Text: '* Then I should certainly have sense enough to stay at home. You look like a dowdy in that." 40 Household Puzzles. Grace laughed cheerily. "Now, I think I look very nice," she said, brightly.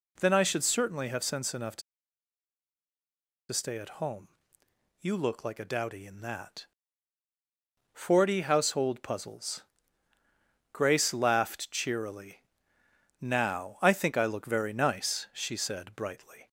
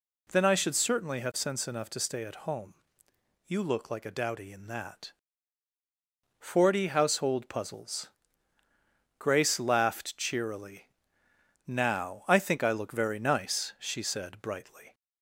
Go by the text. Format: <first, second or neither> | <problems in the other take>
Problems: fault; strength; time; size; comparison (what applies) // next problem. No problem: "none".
second | pauses between "to" and "stay"; strong; at 1.8 s; 1.7 s long